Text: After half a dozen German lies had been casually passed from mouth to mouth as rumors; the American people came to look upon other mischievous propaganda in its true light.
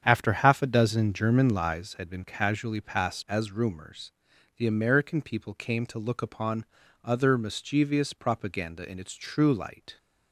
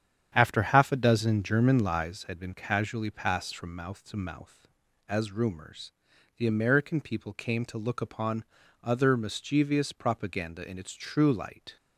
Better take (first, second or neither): second